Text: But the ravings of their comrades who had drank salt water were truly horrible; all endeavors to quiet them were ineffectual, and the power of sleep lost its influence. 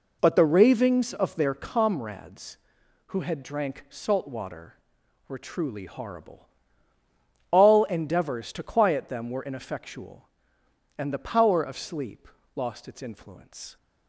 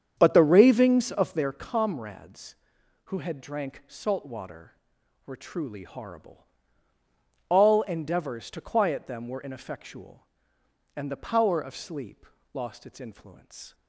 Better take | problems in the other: first | starts louder than the rest; strong; until 1.4 s; 8 dB // pauses between "sleep" and "lost"; slight; at 12.2 s; 0.26 s long; slight in the first

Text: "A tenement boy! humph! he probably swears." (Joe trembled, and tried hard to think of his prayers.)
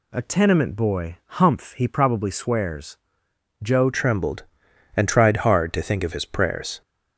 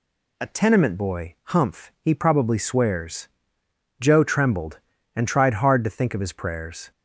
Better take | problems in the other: second | changes voice at "trembled"; from 3.9 s on; 2.9 s long

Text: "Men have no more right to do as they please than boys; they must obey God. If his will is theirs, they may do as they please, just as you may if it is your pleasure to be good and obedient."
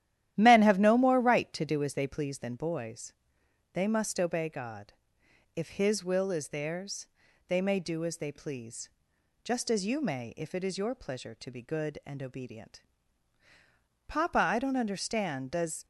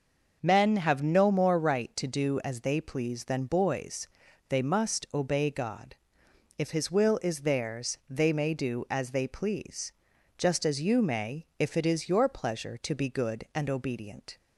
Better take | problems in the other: second | starts louder than the rest; strong; until 1.3 s; 12.5 dB; also in the second // goes on to say "Papa I don't understand Does"; strong; from 14.0 s on; 1.7 s long

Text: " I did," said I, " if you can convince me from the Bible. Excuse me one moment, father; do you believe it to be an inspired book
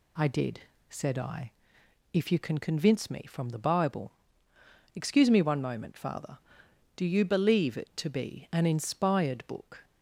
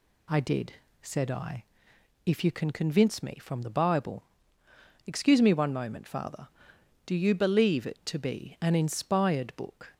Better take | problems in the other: neither | none

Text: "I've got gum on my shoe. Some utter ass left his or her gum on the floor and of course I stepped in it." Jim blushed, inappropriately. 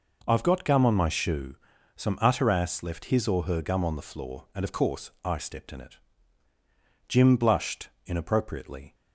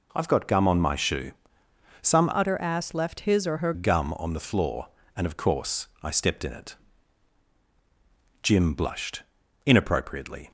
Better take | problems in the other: first | changes voice from "utter" to "her"; from 2.3 to 3.7 s; 1.4 s long

